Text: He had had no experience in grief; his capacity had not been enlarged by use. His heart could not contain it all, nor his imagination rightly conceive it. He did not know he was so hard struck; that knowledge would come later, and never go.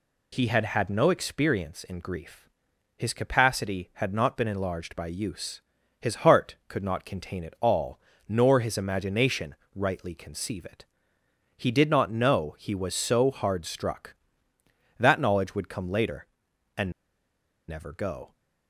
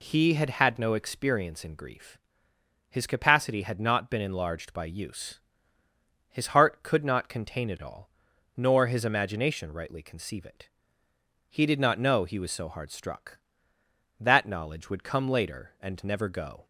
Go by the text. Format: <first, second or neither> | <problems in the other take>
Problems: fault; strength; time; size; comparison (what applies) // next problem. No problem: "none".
second | pauses between "imagination" and "rightly"; slight; at 9.5 s; 0.22 s long // pauses between "and" and "never"; noticeable; at 16.9 s; 0.76 s long